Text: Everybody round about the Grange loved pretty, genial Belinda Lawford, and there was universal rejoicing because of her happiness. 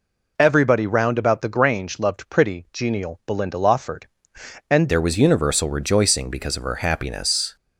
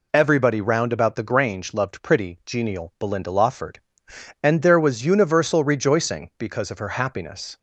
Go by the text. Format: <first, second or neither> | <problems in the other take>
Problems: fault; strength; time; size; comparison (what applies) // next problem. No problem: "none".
second | changes voice at "there"; from 4.8 s on; 2.7 s long